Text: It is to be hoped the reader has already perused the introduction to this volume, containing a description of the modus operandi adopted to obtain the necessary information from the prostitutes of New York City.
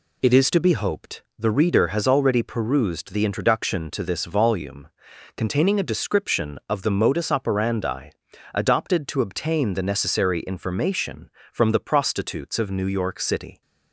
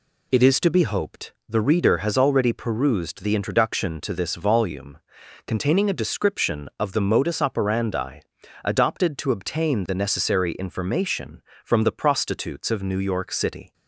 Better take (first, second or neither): neither